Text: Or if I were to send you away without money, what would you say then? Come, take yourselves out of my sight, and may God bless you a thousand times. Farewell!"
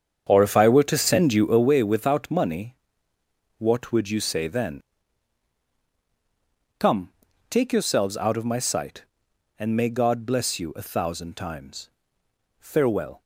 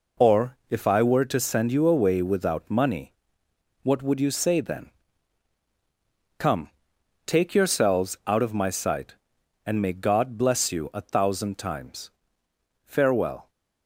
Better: second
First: starts louder than the rest; strong; until 1.7 s; 8 dB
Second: none

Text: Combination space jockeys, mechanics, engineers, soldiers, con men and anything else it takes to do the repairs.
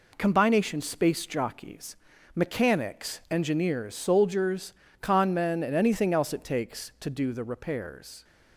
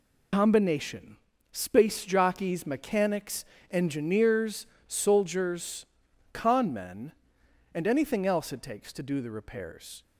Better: first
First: none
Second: loses the start of "Combination"; at 0.3 s; 70 ms // pauses between "Combination" and "space"; at 1.1 s; 0.38 s long

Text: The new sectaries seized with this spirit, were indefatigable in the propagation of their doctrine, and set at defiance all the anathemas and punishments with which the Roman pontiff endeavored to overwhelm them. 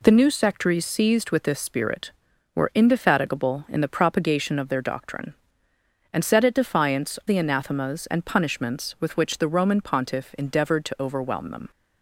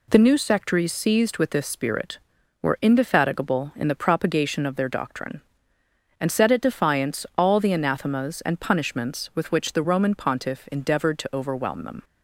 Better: second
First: skips "all"; at 7.2 s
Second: none

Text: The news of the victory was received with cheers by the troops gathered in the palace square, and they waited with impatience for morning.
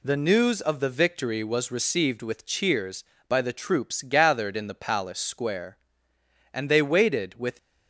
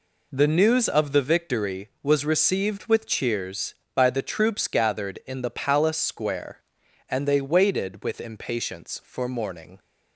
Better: second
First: stops before "impatience for morning"; at 7.5 s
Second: none

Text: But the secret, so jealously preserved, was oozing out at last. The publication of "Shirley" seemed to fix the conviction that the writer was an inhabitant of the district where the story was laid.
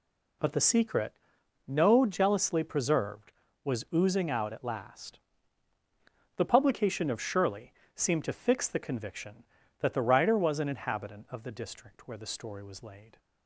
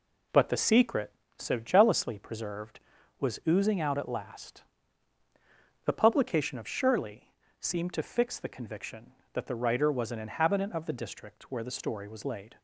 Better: second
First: says "no" for "so"; at 1.6 s // pauses between "Shirley" and "seemed"; slight; at 7.7 s; 0.20 s long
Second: pauses between "Shirley" and "seemed"; slight; at 7.3 s; 0.30 s long

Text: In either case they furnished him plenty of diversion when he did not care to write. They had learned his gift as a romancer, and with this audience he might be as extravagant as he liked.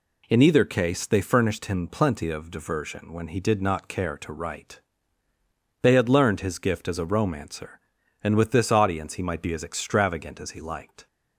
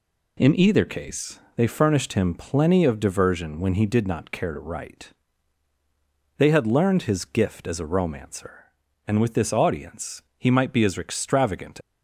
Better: first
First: none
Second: pauses between "case" and "they"; slight; at 1.4 s; 0.16 s long // pauses between "audience" and "he"; slight; at 10.2 s; 0.16 s long // stops before "as he liked"; at 11.8 s

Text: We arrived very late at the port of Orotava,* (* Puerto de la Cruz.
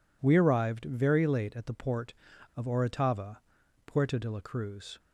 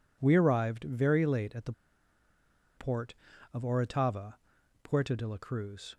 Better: first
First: none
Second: pauses between "the" and "port"; at 1.7 s; 1.0 s long

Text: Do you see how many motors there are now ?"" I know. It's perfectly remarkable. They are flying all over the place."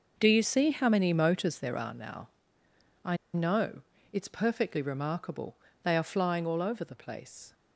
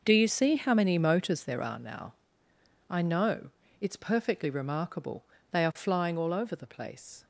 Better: second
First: pauses between "I" and "know"; slight; at 3.1 s; 0.18 s long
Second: none

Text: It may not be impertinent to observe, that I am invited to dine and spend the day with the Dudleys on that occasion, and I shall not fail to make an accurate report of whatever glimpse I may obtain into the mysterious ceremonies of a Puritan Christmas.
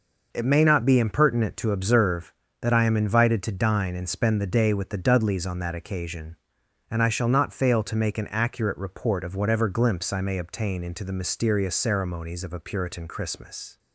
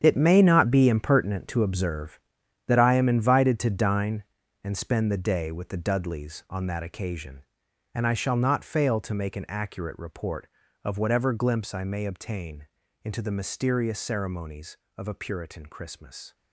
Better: first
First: none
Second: gets quieter; strong; throughout; 12.5 dB // pauses between "obtain" and "into"; at 12.6 s; 0.38 s long

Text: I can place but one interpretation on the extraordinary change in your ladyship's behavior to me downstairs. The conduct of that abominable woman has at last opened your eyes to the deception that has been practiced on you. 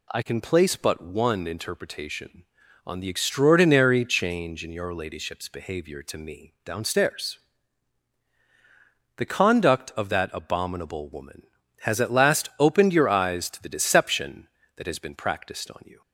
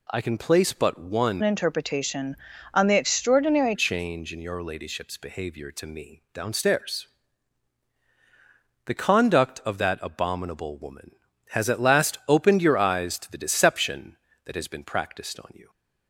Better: first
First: none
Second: changes voice from "interpretation" to "extraordinary"; from 1.4 to 3.7 s; 2.3 s long

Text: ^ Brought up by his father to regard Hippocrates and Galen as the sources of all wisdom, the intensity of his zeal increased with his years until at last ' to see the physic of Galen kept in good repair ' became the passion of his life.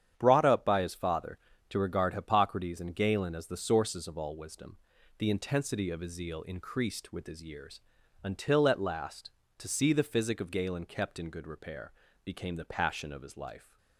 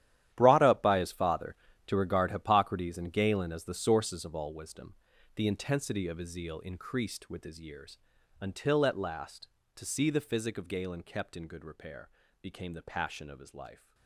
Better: first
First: starts louder than the rest; strong; until 1.1 s; 9 dB // pauses between "years" and "until"; at 7.8 s; 0.42 s long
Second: gets quieter; strong; throughout; 17 dB // starts louder than the rest; strong; until 1.3 s; 12 dB // pauses between "years" and "until"; at 7.9 s; 0.42 s long

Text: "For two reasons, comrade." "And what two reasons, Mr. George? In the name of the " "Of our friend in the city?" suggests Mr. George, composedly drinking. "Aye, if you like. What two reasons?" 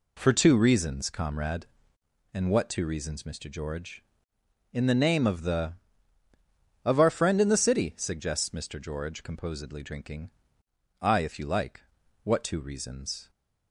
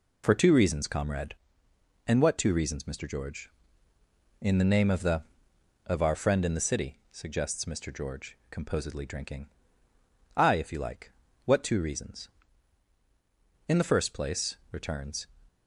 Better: first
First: none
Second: goes on to say "In the first place returns"; from 13.6 s on; 1.5 s long

